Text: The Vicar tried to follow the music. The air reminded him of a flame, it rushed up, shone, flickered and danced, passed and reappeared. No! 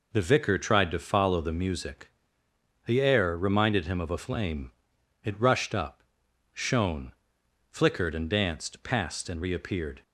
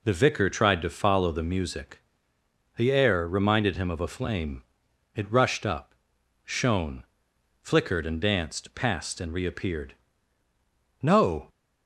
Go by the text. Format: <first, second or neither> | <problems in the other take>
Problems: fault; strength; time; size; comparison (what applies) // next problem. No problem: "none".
second | stops before "No"; at 10.0 s